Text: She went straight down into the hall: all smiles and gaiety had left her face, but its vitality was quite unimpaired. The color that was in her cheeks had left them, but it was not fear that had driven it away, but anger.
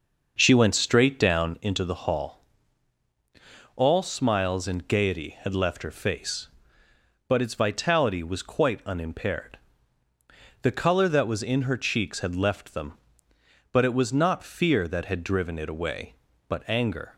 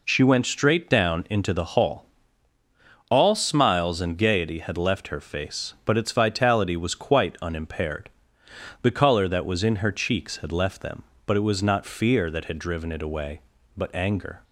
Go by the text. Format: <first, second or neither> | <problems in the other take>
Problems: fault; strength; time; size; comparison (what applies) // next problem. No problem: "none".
second | starts louder than the rest; noticeable; until 1.6 s; 6 dB